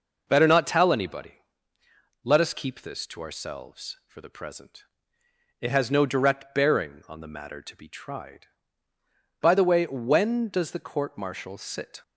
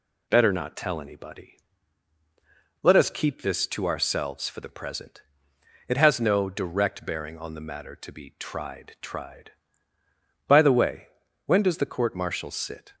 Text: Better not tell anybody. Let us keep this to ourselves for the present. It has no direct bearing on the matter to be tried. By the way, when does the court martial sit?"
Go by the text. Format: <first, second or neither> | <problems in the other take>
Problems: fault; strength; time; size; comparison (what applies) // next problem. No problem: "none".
first | says "tried" twice; at 9.0 s